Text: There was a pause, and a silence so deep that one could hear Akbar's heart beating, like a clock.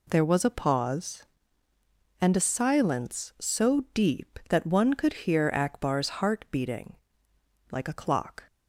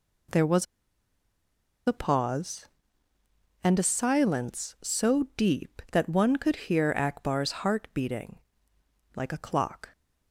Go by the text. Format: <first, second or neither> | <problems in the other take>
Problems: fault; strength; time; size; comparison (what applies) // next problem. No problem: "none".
first | pauses between "was" and "a"; at 0.6 s; 1.2 s long